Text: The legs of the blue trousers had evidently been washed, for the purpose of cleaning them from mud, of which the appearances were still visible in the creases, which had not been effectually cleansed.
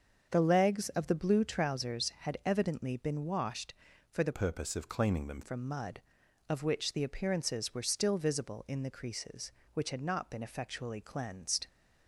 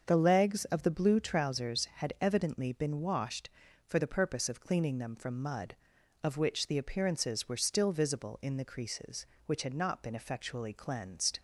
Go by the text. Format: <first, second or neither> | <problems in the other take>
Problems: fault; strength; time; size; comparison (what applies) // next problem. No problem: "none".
second | starts louder than the rest; until 1.3 s; 6.5 dB; also in the second // changes voice from "purpose" to "them"; from 4.3 to 5.4 s; 1.1 s long